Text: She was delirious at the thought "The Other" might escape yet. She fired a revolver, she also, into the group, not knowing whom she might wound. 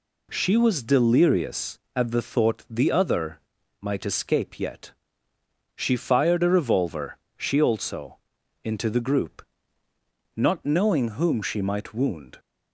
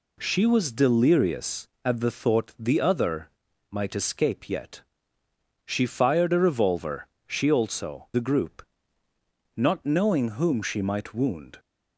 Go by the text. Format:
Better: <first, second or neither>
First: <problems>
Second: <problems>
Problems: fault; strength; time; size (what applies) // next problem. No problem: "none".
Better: first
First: pauses between "Other" and "might"; at 3.3 s; 0.42 s long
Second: pauses between "Other" and "might"; at 3.2 s; 0.42 s long // skips "into"; at 8.1 s